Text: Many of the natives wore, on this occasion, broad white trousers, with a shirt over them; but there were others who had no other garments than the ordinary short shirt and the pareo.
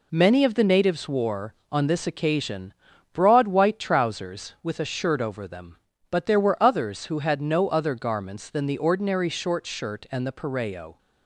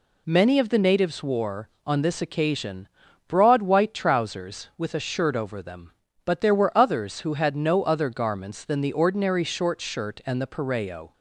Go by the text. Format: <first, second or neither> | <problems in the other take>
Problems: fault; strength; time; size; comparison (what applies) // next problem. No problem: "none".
second | gets quieter; noticeable; throughout; 5.5 dB